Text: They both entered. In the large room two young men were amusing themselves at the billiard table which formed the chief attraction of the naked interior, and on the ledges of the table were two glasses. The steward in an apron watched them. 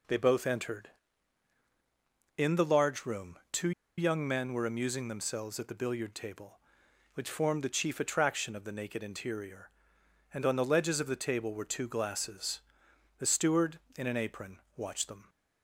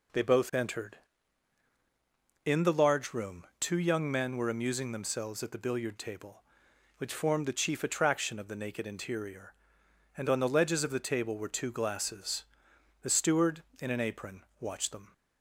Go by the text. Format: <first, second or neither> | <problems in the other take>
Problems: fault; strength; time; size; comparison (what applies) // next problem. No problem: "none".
second | pauses between "two" and "young"; slight; at 3.7 s; 0.27 s long // pauses between "apron" and "watched"; slight; at 14.5 s; 0.16 s long; slight in the second